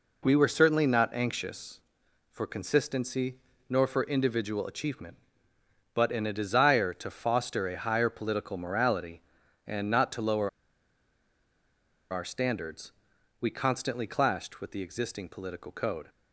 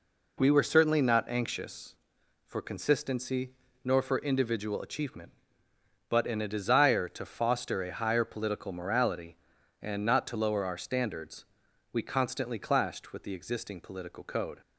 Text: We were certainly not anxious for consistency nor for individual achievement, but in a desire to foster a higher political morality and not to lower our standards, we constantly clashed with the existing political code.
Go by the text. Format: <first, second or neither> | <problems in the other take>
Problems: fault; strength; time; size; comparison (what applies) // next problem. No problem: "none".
second | pauses between "consistency" and "nor"; slight; at 3.3 s; 0.32 s long; slight in the second // pauses between "lower" and "our"; strong; at 10.4 s; 1.6 s long